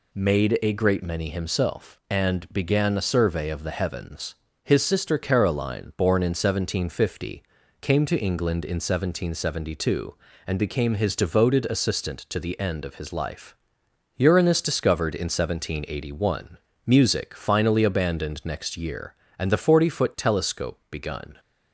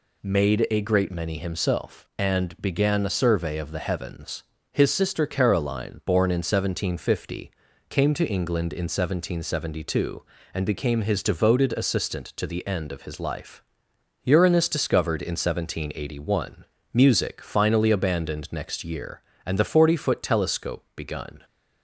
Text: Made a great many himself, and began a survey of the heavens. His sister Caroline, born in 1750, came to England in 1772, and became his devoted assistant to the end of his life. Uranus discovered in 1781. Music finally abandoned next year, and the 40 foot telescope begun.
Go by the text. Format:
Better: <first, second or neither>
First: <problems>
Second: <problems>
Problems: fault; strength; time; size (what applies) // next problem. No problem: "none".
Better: neither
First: none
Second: none